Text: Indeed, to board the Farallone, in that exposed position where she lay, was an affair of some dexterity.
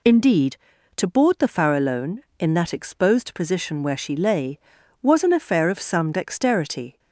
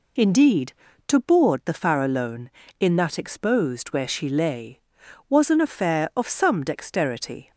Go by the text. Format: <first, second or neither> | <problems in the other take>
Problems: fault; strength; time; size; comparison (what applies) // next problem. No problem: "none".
first | skips "position"; at 3.8 s